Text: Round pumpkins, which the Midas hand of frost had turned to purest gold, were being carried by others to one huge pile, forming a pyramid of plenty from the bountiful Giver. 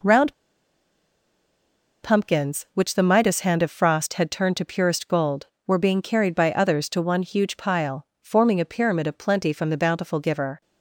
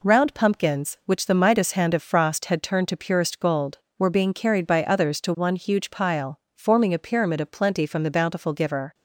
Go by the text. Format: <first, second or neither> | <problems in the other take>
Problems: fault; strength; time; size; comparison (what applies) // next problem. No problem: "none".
second | pauses between "Round" and "pumpkins"; strong; at 0.3 s; 1.6 s long